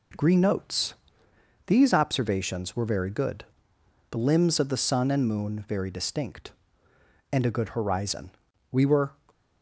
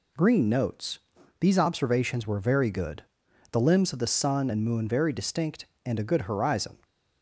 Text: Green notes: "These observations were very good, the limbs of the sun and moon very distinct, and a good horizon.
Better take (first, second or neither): second